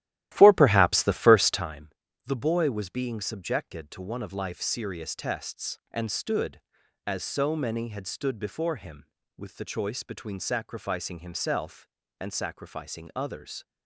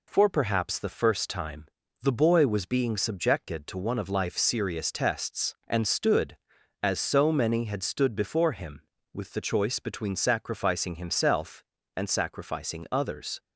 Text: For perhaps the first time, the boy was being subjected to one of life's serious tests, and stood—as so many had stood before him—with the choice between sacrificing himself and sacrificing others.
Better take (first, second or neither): second